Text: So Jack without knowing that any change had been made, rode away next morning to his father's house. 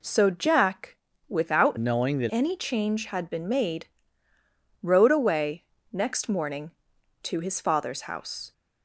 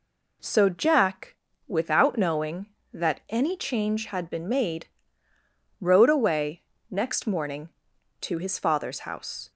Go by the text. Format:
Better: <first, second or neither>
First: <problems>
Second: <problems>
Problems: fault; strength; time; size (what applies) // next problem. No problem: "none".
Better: second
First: pauses between "Jack" and "without"; slight; at 0.9 s; 0.32 s long // changes voice from "knowing" to "that"; from 1.7 to 2.3 s; 0.6 s long // pauses between "away" and "next"; slight; at 5.6 s; 0.26 s long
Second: pauses between "Jack" and "without"; slight; at 1.3 s; 0.32 s long // pauses between "away" and "next"; slight; at 6.6 s; 0.26 s long